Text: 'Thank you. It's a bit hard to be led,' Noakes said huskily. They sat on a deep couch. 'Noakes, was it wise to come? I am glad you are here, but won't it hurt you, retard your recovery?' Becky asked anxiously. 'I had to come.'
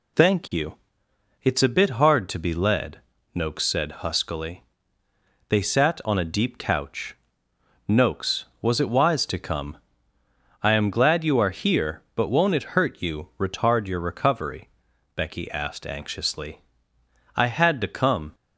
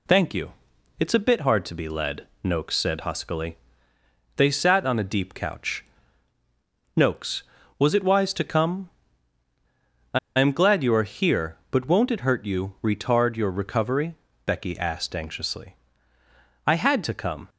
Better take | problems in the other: first | pauses between "I" and "am"; slight; at 10.1 s; 0.19 s long

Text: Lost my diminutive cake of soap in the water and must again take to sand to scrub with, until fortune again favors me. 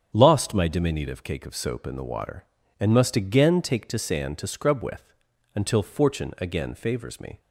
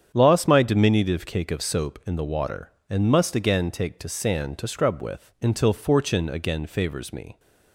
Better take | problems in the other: neither | starts louder than the rest; strong; the same in both

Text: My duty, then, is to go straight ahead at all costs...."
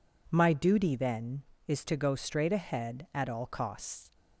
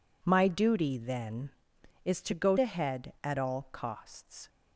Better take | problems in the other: first | skips "straight"; at 2.5 s

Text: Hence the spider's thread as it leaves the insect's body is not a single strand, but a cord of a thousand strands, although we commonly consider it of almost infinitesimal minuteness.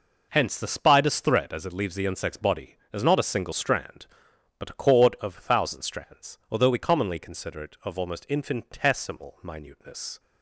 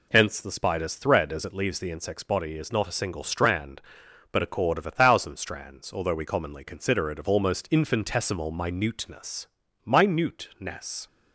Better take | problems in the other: first | says "minuteness" twice; at 9.8 s

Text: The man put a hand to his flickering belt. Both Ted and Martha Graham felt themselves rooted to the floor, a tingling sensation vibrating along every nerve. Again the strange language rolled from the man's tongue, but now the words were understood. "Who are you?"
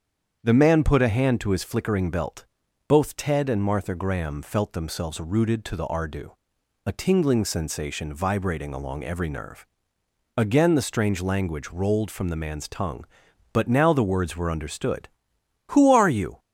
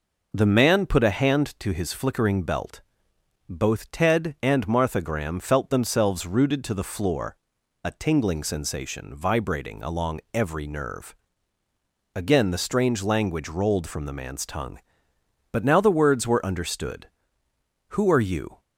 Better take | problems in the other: second | starts louder than the rest; strong; until 1.4 s; 7.5 dB // says "ardu" for "floor"; at 5.8 s

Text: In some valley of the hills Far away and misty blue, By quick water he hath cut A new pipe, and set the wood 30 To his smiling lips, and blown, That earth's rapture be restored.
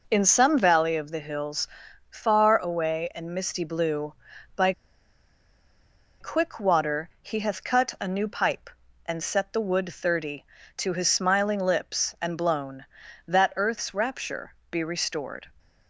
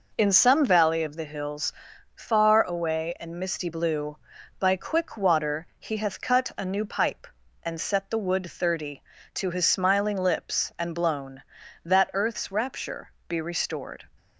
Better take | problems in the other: second | pauses between "hills" and "Far"; noticeable; at 1.6 s; 0.46 s long; noticeable in the second // pauses between "By" and "quick"; strong; at 4.7 s; 1.4 s long // pauses between "rapture" and "be"; slight; at 14.5 s; 0.16 s long; slight in the second

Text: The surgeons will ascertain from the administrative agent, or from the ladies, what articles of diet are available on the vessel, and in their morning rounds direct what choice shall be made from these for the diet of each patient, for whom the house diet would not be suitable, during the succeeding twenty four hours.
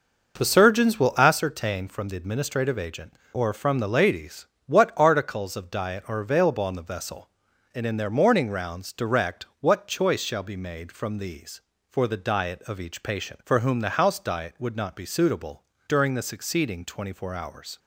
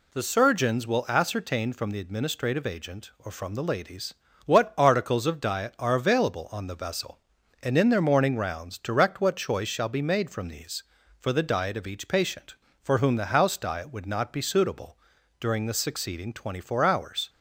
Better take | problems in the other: second | starts louder than the rest; noticeable; until 1.4 s; 5.5 dB

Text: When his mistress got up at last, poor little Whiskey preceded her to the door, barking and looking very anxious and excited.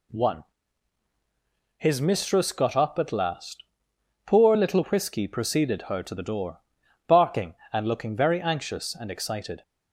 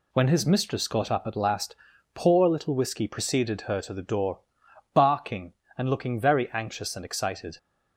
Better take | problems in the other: second | says "One" for "When"; at 0.0 s

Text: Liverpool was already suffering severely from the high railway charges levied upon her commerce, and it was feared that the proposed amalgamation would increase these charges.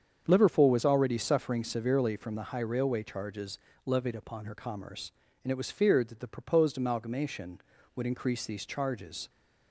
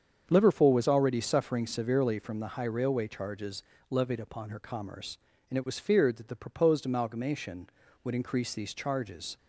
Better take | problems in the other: neither | starts louder than the rest; strong; the same in both // pauses between "charges" and "levied"; slight; the same in both

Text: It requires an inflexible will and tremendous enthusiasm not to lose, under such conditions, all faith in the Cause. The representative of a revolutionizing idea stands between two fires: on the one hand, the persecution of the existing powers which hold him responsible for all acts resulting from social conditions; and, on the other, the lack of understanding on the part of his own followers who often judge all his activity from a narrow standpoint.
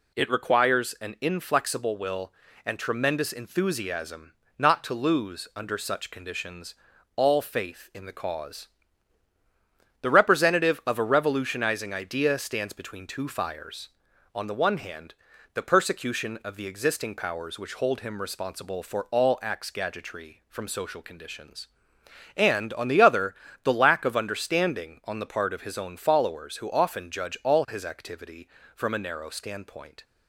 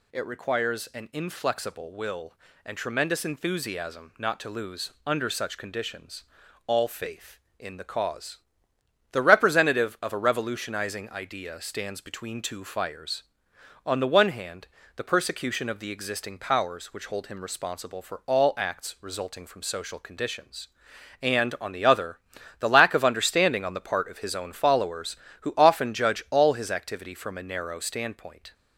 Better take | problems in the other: second | pauses between "enthusiasm" and "not"; slight; at 4.3 s; 0.26 s long // says "gadgetry" for "resulting"; at 19.7 s

